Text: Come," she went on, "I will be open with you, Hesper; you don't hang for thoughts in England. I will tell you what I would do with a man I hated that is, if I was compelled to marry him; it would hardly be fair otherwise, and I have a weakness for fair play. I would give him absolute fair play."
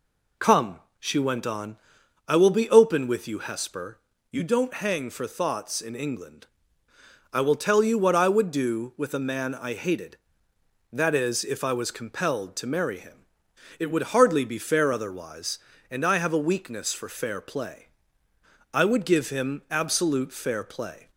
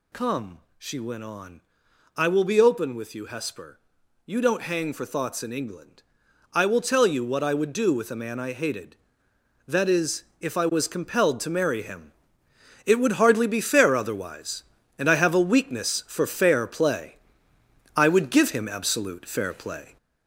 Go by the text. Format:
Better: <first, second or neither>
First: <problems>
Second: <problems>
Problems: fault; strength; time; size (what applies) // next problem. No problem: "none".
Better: first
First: none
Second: gets louder; noticeable; throughout; 4.5 dB